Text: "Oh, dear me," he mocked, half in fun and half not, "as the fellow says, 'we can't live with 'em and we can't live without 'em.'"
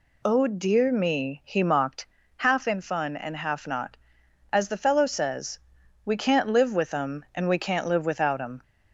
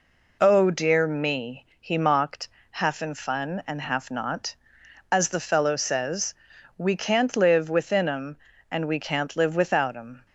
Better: first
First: none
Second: says "within" for "with"; at 7.6 s

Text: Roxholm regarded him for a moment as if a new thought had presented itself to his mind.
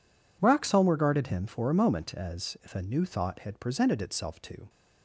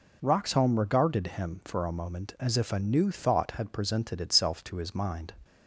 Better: second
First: stops before "his mind"; at 4.6 s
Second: none

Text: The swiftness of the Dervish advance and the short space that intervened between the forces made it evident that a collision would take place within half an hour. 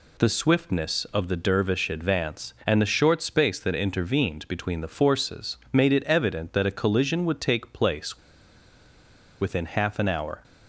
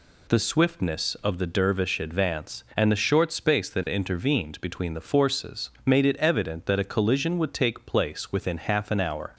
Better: second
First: pauses between "place" and "within"; at 8.1 s; 1.2 s long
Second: none

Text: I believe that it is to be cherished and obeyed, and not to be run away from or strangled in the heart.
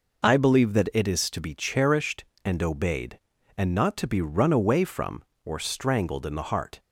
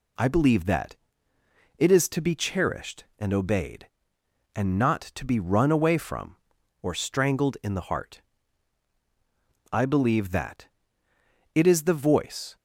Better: first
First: none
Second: pauses between "that" and "it"; noticeable; at 0.9 s; 0.82 s long // goes on to say "I believe that it is the voice"; strong; from 9.7 s on; 2.8 s long

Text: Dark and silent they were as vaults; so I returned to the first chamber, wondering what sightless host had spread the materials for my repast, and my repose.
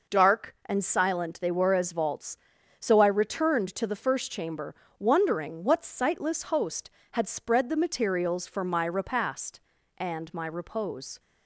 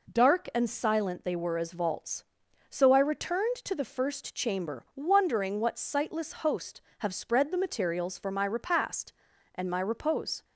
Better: first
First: none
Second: says "have" for "had"; at 6.9 s

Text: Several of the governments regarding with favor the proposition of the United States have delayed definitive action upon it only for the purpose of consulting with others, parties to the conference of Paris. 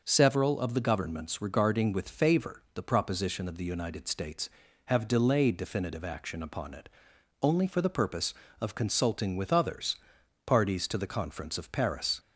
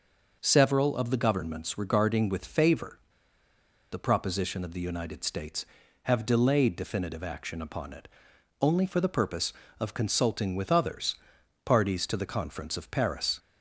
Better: first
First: pauses between "it" and "only"; noticeable; at 6.8 s; 0.54 s long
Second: pauses between "favor" and "the"; noticeable; at 2.9 s; 0.92 s long // pauses between "it" and "only"; noticeable; at 8.0 s; 0.54 s long

